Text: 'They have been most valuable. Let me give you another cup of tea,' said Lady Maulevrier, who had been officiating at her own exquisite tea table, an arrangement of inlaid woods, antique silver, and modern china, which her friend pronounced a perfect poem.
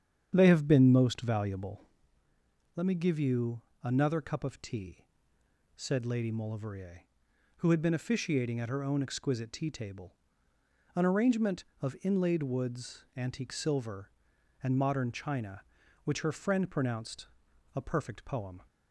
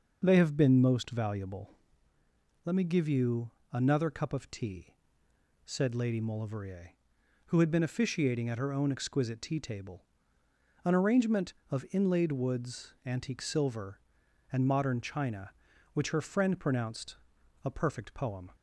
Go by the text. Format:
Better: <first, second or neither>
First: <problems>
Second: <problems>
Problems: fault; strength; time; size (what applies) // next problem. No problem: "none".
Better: second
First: starts louder than the rest; strong; until 2.0 s; 8.5 dB // pauses between "you" and "another"; slight; at 3.6 s; 0.22 s long // pauses between "pronounced" and "a"; noticeable; at 17.2 s; 0.48 s long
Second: pauses between "you" and "another"; slight; at 3.5 s; 0.22 s long // pauses between "pronounced" and "a"; noticeable; at 17.1 s; 0.48 s long